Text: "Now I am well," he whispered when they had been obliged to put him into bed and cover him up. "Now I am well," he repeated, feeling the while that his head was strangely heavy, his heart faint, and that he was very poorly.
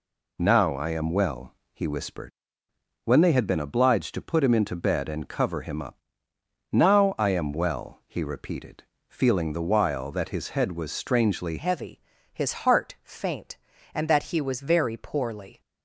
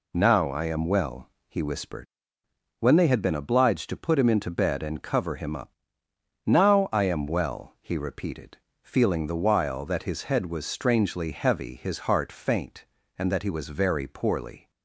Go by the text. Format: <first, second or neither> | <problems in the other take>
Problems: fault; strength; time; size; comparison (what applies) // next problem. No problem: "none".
second | pauses between "whispered" and "when"; noticeable; at 2.3 s; 0.76 s long; noticeable in the second // changes voice at "heavy"; from 11.5 s on; 4.1 s long